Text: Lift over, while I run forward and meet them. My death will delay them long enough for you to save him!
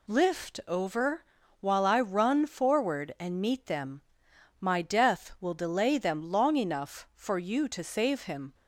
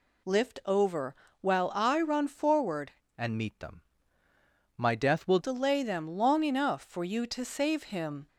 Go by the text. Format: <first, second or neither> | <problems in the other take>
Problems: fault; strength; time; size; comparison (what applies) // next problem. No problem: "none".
first | changes voice from "and" to "will"; from 3.1 to 5.3 s; 2.2 s long